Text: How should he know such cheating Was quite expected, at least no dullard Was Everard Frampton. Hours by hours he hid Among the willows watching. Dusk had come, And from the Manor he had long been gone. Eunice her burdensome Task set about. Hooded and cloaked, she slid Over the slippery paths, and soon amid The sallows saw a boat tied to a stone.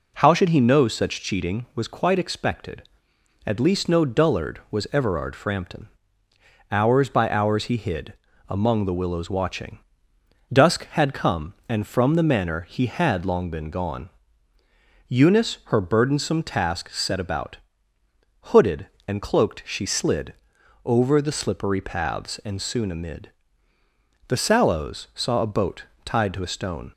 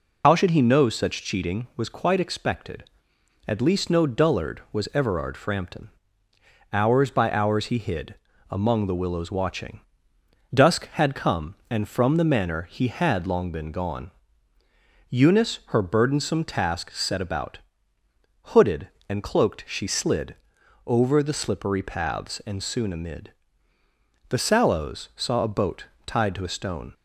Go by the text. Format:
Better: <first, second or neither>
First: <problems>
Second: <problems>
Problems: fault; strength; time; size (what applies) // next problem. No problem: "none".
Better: first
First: pauses between "hid" and "Among"; slight; at 8.1 s; 0.34 s long // pauses between "slid" and "Over"; noticeable; at 20.3 s; 0.52 s long // pauses between "amid" and "The"; noticeable; at 23.2 s; 0.98 s long // pauses between "boat" and "tied"; slight; at 25.8 s; 0.20 s long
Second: loses the start of "How"; at 0.2 s; 75 ms // pauses between "hid" and "Among"; slight; at 8.1 s; 0.34 s long // pauses between "slid" and "Over"; noticeable; at 20.3 s; 0.52 s long // pauses between "amid" and "The"; noticeable; at 23.3 s; 0.98 s long // pauses between "boat" and "tied"; slight; at 25.8 s; 0.20 s long